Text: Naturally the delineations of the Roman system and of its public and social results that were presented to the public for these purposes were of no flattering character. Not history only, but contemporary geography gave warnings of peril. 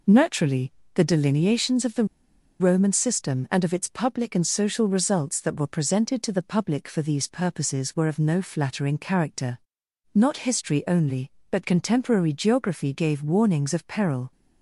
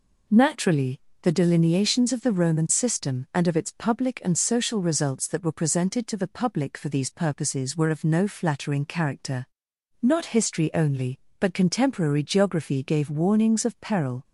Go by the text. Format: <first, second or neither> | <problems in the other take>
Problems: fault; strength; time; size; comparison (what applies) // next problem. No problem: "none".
second | pauses between "Naturally" and "the"; slight; at 0.7 s; 0.22 s long; slight in the second // pauses between "the" and "Roman"; noticeable; at 2.0 s; 0.55 s long